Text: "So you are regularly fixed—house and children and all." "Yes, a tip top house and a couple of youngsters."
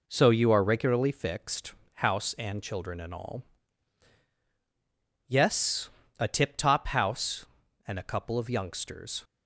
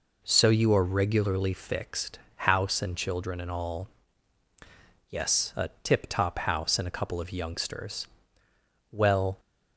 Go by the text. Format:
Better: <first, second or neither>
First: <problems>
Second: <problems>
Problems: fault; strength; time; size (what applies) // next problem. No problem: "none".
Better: first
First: none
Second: goes on to say "Well"; slight; from 8.9 s on; 0.48 s long